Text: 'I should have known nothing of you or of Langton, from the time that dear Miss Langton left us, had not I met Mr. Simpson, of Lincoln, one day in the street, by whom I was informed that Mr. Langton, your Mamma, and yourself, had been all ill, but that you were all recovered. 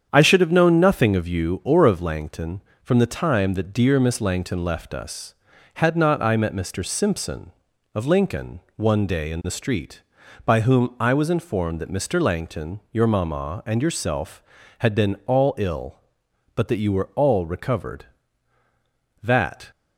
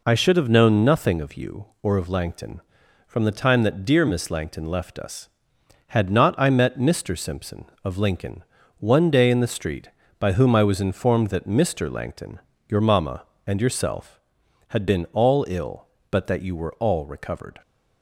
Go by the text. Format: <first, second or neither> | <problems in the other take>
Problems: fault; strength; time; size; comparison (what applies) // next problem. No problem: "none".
second | starts louder than the rest; strong; until 1.1 s; 8 dB // goes on to say "That"; slight; from 19.2 s on; 0.46 s long